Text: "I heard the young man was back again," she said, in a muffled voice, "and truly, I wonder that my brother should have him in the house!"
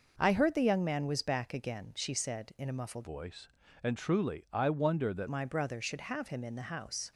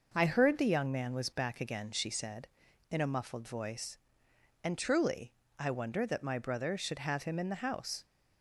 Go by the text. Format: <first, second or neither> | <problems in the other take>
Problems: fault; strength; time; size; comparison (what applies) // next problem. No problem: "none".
second | changes voice from "voice" to "that"; from 3.0 to 5.2 s; 2.2 s long